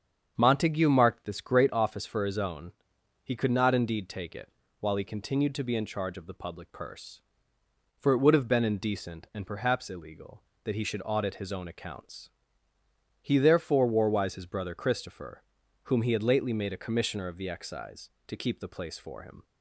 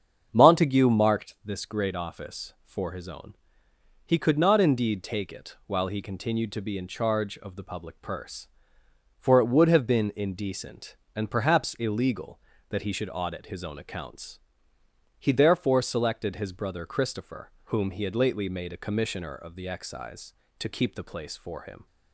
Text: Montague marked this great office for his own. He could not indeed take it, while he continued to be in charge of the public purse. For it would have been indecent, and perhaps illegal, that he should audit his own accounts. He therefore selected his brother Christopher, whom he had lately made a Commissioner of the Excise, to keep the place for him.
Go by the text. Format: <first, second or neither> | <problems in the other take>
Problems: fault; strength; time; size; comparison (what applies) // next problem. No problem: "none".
second | starts louder than the rest; strong; until 1.3 s; 7.5 dB; strong in the second // says "warwise" for "selected"; at 13.8 s